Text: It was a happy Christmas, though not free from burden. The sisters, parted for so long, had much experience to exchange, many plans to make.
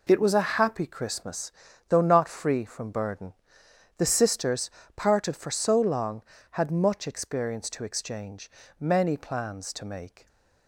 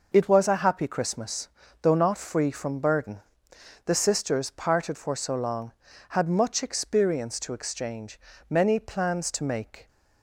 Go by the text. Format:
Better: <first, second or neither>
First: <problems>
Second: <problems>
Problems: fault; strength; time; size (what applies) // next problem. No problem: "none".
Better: neither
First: none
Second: none